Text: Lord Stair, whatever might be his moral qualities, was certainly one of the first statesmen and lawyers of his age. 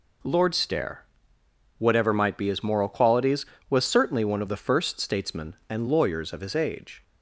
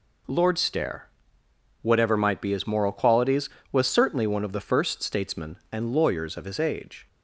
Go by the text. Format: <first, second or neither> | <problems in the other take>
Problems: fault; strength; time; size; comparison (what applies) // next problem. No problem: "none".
neither | none